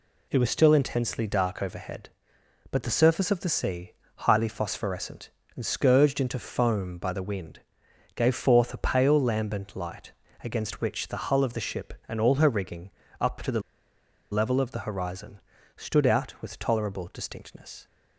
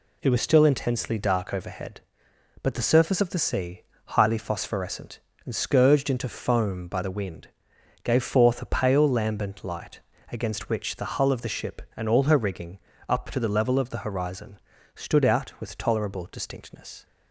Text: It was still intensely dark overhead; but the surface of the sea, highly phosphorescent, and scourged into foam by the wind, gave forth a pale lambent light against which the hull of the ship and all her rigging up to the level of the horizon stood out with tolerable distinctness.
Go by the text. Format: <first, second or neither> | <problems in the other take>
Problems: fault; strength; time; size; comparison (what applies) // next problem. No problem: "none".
second | pauses between "light" and "against"; slight; at 10.1 s; 0.32 s long; slight in the second // pauses between "rigging" and "up"; slight; at 12.9 s; 0.28 s long; slight in the second // pauses between "the" and "level"; noticeable; at 13.6 s; 0.72 s long // pauses between "horizon" and "stood"; slight; at 15.3 s; 0.36 s long; slight in the second